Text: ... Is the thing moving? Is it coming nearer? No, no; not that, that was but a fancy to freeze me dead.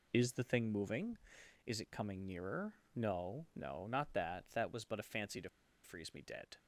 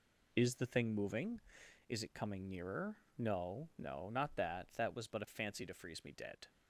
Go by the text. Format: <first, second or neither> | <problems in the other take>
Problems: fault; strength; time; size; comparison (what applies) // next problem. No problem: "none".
second | pauses between "to" and "freeze"; slight; at 5.4 s; 0.34 s long